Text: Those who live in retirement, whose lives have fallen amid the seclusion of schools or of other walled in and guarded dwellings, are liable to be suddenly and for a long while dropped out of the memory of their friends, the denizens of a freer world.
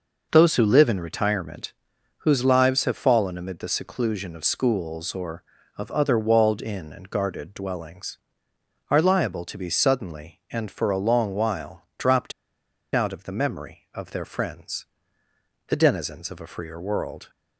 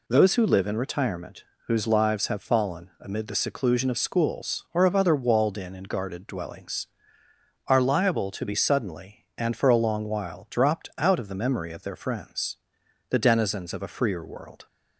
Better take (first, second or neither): second